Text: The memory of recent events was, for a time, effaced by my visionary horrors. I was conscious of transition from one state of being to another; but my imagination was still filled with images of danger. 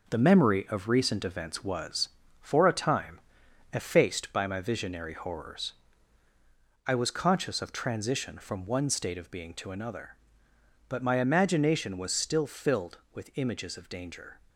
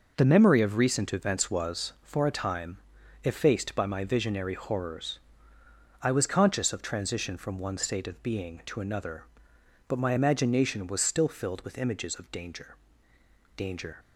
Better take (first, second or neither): first